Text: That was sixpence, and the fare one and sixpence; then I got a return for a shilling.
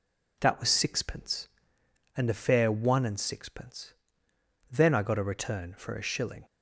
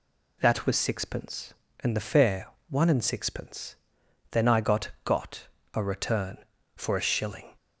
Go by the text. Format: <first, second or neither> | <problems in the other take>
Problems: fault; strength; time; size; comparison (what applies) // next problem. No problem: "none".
first | pauses between "fare" and "one"; slight; at 2.4 s; 0.24 s long // says "got" twice; at 5.0 s